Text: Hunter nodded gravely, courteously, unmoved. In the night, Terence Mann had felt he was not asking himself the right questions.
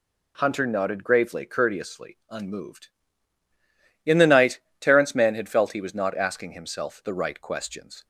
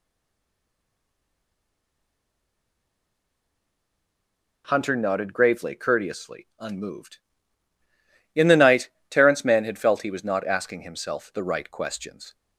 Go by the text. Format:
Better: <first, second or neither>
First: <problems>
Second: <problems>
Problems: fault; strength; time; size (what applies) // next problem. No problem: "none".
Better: first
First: none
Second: stays silent before the first word; strong; until 4.6 s; 4.6 s long